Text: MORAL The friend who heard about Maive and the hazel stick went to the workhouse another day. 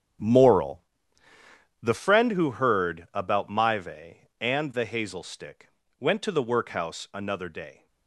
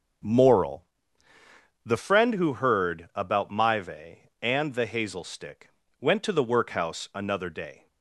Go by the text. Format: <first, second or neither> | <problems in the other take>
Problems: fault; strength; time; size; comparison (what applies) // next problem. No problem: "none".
second | gets quieter; strong; throughout; 14 dB // starts louder than the rest; strong; until 2.2 s; 9.5 dB; strong in the second // pauses between "MORAL" and "The"; at 0.8 s; 1.0 s long; also in the second // pauses between "stick" and "went"; slight; at 5.7 s; 0.28 s long; slight in the second